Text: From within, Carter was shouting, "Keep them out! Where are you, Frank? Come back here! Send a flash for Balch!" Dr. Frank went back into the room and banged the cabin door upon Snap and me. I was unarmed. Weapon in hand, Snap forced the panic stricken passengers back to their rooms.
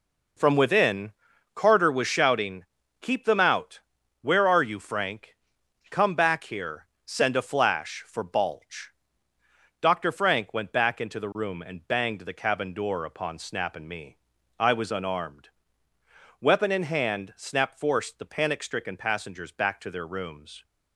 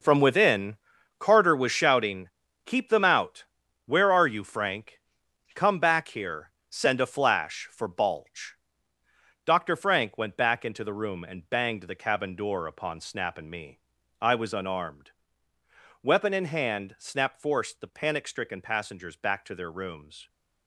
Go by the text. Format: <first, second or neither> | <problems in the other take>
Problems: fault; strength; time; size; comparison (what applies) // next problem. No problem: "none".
first | gets quieter; strong; throughout; 11.5 dB